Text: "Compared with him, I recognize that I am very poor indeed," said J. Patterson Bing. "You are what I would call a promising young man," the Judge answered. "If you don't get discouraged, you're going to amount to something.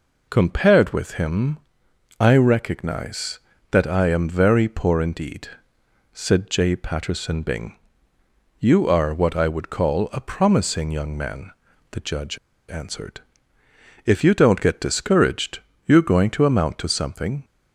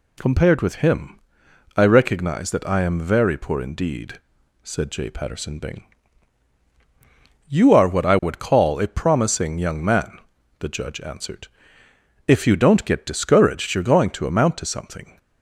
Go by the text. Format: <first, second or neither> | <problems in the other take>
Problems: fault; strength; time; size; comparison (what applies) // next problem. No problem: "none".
second | pauses between "Judge" and "answered"; slight; at 12.3 s; 0.31 s long